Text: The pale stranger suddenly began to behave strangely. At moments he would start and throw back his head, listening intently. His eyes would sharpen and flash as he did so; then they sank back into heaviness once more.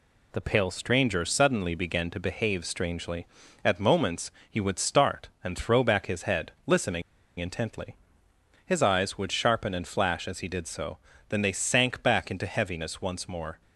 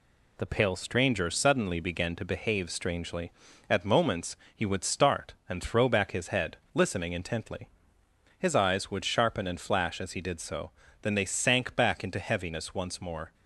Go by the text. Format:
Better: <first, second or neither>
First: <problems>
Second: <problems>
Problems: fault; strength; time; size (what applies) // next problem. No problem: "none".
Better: second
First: pauses between "moments" and "he"; slight; at 4.2 s; 0.20 s long // pauses between "listening" and "intently"; at 7.0 s; 0.36 s long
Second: pauses between "moments" and "he"; slight; at 4.3 s; 0.20 s long